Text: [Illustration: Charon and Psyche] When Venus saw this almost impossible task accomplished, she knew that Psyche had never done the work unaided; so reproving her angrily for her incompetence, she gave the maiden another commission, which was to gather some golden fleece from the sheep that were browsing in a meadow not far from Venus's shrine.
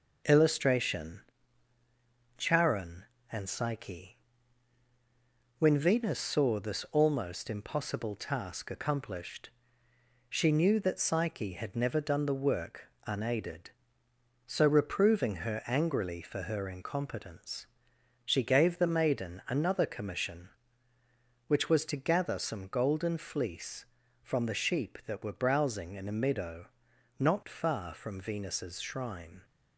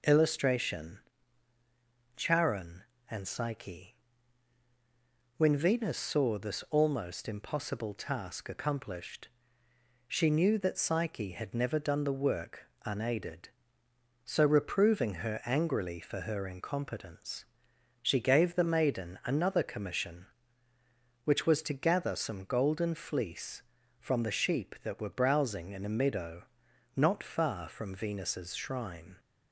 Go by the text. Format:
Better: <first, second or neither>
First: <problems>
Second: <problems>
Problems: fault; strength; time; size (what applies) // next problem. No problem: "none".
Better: second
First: gets quieter; slight; throughout; 3 dB // pauses between "Psyche" and "When"; strong; at 4.1 s; 1.4 s long // pauses between "work" and "unaided"; slight; at 12.9 s; 0.16 s long // pauses between "meadow" and "not"; noticeable; at 26.6 s; 0.52 s long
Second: pauses between "Psyche" and "When"; strong; at 3.9 s; 1.4 s long // pauses between "work" and "unaided"; slight; at 12.6 s; 0.16 s long // pauses between "meadow" and "not"; noticeable; at 26.4 s; 0.52 s long